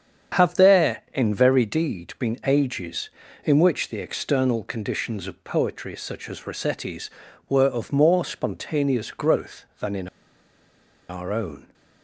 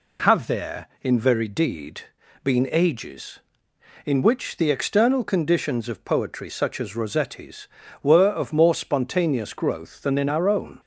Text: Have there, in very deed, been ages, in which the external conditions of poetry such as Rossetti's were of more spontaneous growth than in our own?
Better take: second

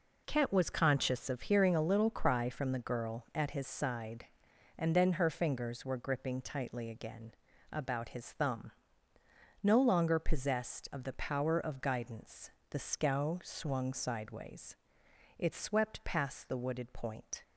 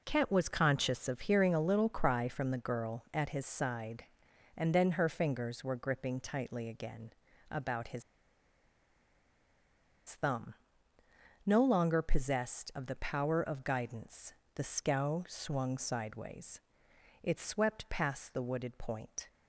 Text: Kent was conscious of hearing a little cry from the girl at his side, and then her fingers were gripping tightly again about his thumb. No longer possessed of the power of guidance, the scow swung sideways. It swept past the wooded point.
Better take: first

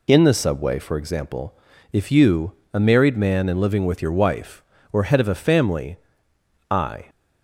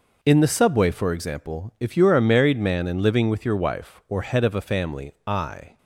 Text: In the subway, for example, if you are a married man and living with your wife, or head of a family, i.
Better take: second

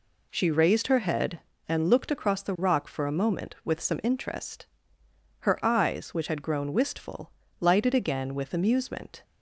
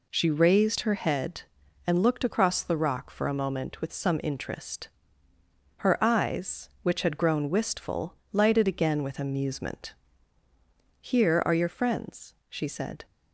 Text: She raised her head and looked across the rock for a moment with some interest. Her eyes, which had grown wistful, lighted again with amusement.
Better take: first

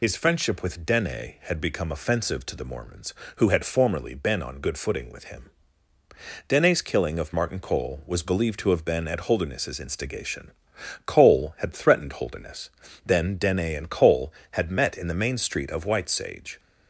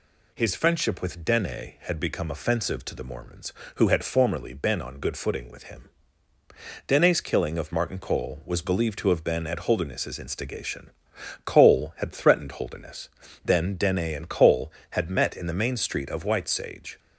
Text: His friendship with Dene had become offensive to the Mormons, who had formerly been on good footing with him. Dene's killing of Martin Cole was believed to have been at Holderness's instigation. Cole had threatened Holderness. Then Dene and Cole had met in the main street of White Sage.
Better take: second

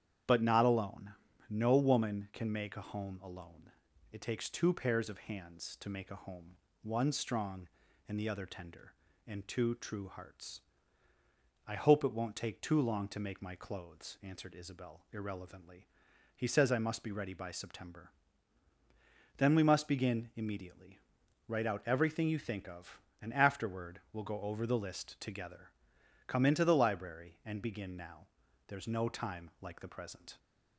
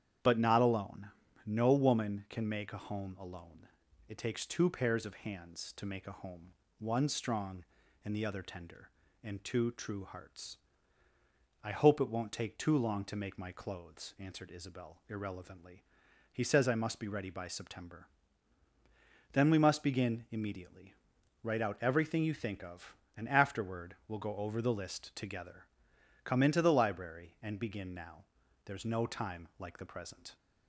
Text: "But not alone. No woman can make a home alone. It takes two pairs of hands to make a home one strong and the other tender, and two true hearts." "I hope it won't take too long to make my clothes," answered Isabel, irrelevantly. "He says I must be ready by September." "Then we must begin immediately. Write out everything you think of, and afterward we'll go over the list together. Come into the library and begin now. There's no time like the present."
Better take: neither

